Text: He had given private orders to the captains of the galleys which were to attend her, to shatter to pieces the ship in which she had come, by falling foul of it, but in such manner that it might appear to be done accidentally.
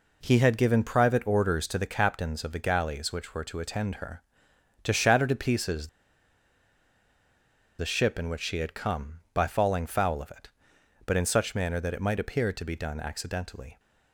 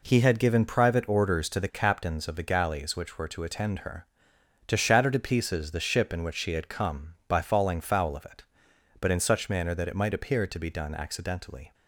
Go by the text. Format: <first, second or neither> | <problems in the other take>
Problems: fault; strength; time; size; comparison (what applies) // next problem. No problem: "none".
second | pauses between "pieces" and "the"; strong; at 5.8 s; 1.9 s long